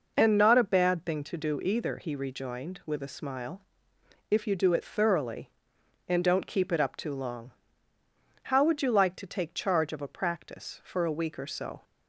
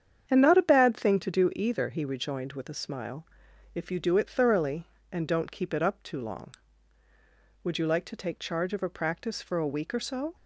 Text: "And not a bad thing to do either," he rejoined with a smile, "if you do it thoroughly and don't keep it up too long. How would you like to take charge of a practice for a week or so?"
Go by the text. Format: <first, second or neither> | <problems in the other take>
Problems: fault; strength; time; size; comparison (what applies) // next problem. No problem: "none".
first | starts louder than the rest; strong; until 1.3 s; 8.5 dB // skips "How"; at 7.0 s